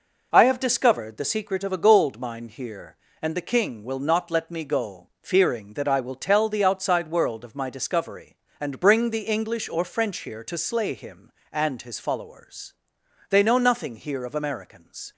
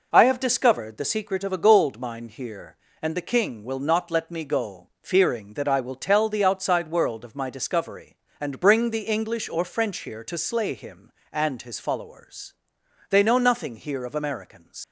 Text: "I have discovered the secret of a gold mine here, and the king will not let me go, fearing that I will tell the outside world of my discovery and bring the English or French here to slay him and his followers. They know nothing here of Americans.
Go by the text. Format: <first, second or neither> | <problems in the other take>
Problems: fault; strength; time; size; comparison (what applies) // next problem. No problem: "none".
first | leaves "Americans" unfinished; at 14.8 s; 85 ms